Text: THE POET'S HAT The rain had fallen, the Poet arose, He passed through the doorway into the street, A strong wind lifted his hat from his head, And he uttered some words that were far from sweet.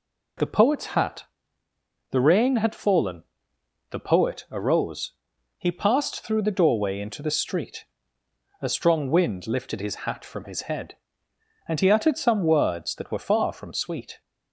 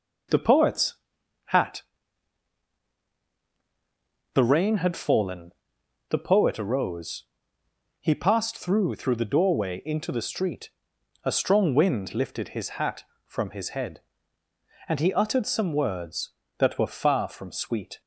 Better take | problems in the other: first | pauses between "POET'S" and "HAT"; noticeable; at 0.9 s; 0.54 s long // pauses between "HAT" and "The"; strong; at 1.8 s; 2.5 s long; noticeable in the first // says "through" twice; at 8.9 s

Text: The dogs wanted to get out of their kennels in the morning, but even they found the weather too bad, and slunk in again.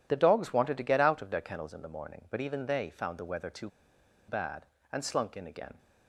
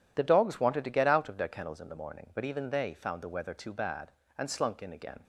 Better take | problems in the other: second | pauses between "too" and "bad"; noticeable; at 3.6 s; 0.60 s long

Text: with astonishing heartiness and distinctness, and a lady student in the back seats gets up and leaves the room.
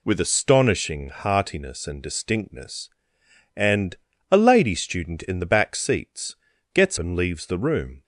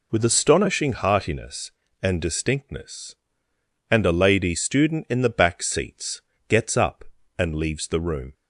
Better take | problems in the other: second | pauses between "and" and "a"; slight; at 3.9 s; 0.36 s long // pauses between "seats" and "gets"; at 6.3 s; 0.38 s long; slight in the second // skips "up"; at 6.9 s

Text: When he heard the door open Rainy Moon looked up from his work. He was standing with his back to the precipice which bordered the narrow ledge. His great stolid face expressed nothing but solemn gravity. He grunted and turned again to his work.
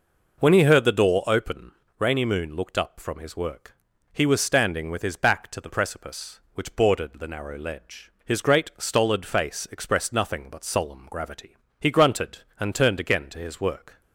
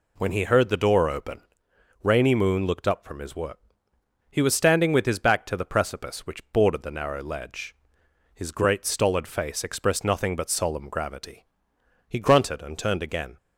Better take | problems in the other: first | pauses between "open" and "Rainy"; noticeable; at 1.4 s; 0.62 s long; slight in the first // stops before "to his work"; at 13.3 s

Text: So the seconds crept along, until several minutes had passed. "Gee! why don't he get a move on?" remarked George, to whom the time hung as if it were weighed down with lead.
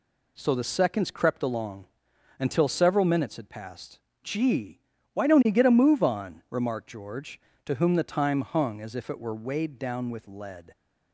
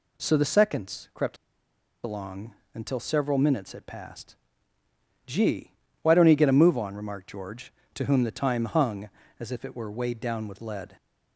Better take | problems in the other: first | pauses between "crept" and "along"; noticeable; at 1.3 s; 0.67 s long

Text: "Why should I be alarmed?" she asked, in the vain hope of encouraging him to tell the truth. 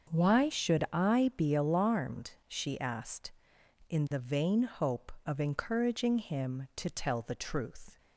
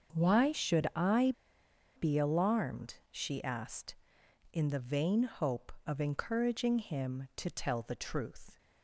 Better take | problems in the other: first | starts louder than the rest; until 1.1 s; 6.5 dB; also in the first // pauses between "I" and "be"; noticeable; at 1.3 s; 0.64 s long

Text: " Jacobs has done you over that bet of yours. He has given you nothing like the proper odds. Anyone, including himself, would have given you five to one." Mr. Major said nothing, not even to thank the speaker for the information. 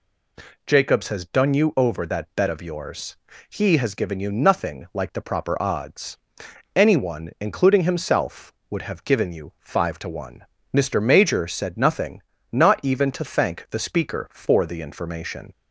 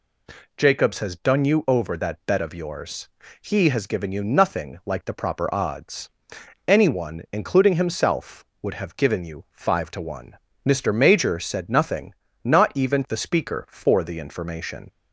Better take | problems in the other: first | skips "to thank"; at 13.0 s

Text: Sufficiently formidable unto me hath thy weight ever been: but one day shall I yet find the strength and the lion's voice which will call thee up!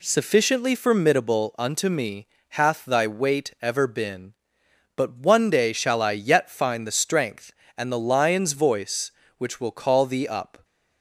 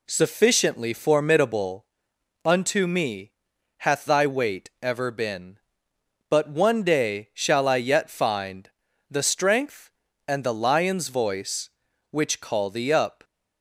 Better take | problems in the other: first | pauses between "formidable" and "unto"; noticeable; at 1.8 s; 0.60 s long // pauses between "me" and "hath"; noticeable; at 3.3 s; 0.46 s long; slight in the first // pauses between "find" and "the"; at 8.6 s; 0.42 s long // skips "will"; at 12.3 s

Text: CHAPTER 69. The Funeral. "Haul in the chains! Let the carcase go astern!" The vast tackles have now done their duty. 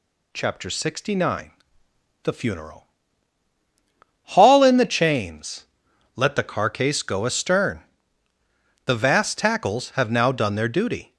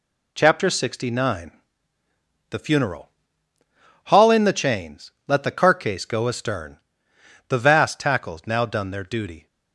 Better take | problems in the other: first | skips "have"; at 8.4 s

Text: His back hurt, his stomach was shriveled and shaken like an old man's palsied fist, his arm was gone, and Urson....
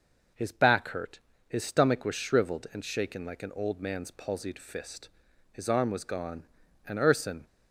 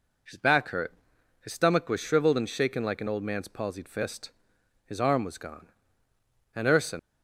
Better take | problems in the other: first | leaves "Urson" unfinished; at 6.9 s; 120 ms

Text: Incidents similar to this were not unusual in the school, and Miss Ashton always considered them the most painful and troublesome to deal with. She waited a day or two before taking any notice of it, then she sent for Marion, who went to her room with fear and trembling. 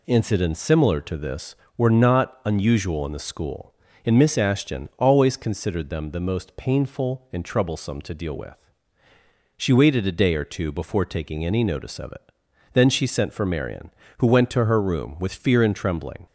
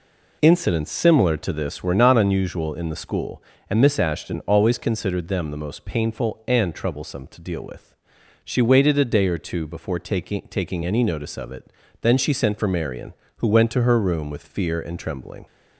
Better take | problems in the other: first | says "taking" twice; at 10.4 s

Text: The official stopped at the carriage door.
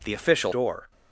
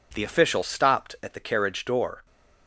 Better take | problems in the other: second | skips "stopped at the carriage"; at 0.5 s

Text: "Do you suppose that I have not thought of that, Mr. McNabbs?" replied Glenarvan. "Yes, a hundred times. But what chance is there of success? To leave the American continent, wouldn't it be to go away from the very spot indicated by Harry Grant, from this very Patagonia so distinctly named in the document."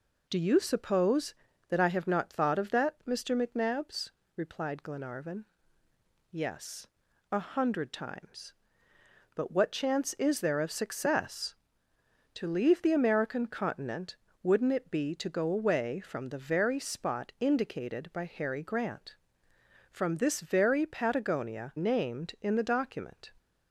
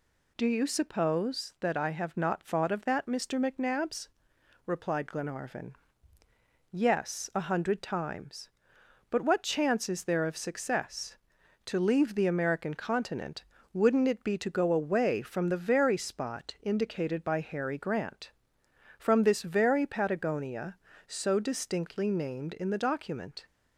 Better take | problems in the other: second | skips "so distinctly"; at 21.7 s

